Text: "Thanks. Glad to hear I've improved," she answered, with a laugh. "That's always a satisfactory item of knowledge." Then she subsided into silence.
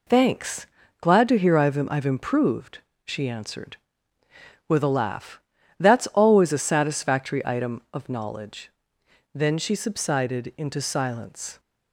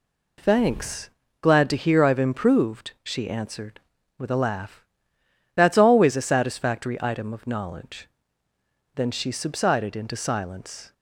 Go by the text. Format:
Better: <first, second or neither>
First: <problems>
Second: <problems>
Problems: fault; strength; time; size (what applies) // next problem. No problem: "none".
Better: second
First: says "I've" twice; at 1.9 s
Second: none